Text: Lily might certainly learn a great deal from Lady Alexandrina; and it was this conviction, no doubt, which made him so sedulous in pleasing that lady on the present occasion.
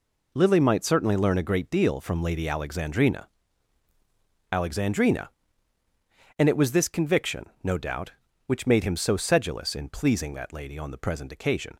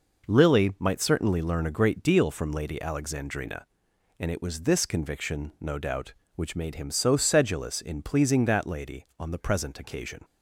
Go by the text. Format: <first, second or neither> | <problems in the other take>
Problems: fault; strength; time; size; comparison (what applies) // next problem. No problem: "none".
second | says "Alexandrina" twice; at 4.5 s